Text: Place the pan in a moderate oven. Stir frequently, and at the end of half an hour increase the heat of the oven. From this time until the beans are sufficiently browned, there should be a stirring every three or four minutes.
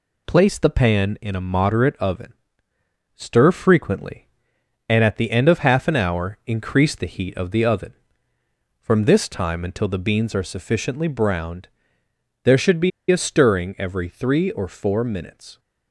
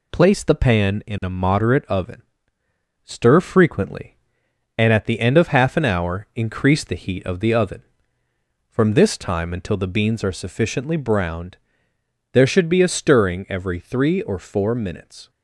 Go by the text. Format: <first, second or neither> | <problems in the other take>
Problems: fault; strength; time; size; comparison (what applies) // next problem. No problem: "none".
second | pauses between "be" and "a"; slight; at 12.9 s; 0.20 s long